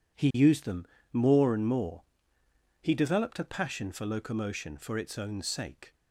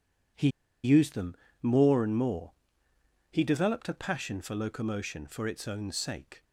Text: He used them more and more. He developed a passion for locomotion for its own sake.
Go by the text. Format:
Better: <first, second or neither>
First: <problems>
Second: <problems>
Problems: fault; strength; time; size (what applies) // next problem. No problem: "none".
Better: first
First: pauses between "them" and "more"; slight; at 0.8 s; 0.26 s long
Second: pauses between "He" and "used"; slight; at 0.4 s; 0.35 s long // pauses between "them" and "more"; slight; at 1.3 s; 0.26 s long